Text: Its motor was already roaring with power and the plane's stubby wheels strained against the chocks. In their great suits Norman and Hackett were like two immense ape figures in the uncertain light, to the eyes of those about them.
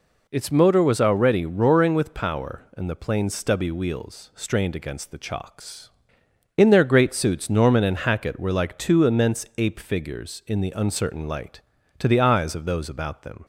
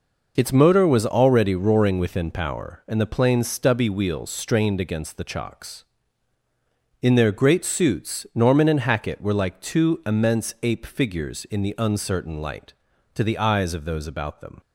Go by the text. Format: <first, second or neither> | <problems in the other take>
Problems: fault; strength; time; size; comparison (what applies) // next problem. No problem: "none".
first | says "within" for "with"; at 1.9 s